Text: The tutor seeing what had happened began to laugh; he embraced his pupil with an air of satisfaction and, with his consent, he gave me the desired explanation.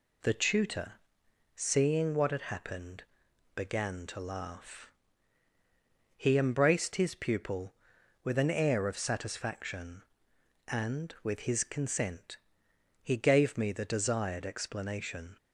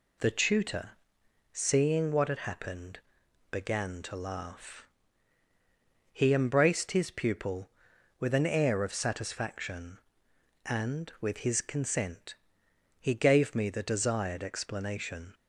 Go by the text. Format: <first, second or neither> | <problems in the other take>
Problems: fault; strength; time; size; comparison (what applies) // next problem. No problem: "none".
neither | pauses between "tutor" and "seeing"; noticeable; the same in both // pauses between "happened" and "began"; noticeable; the same in both